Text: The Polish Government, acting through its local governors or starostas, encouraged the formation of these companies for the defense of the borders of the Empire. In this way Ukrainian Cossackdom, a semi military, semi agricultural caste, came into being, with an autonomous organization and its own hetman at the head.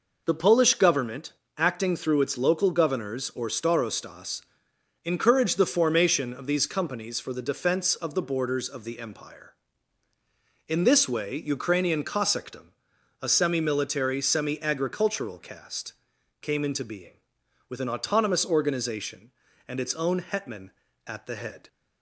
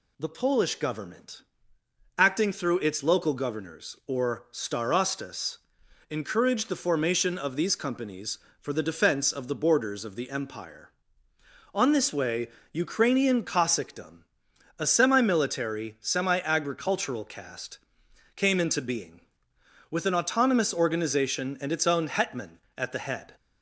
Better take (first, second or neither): first